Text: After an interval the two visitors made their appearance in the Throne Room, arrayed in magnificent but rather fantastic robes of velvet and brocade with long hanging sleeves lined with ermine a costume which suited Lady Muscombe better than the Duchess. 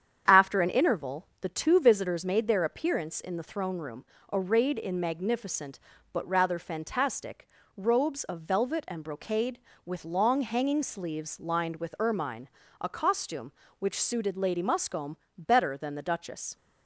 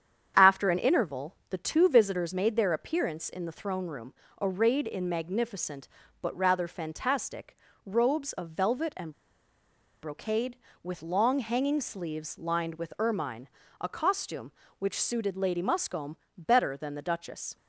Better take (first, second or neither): first